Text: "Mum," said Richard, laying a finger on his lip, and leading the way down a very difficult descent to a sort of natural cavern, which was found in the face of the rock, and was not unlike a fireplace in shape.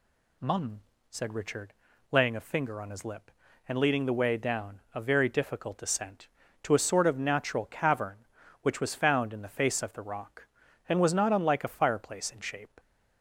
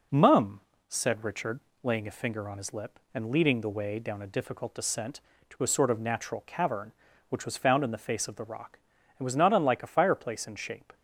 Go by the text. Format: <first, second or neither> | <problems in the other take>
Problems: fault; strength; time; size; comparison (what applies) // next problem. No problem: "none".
first | skips "very"; at 4.2 s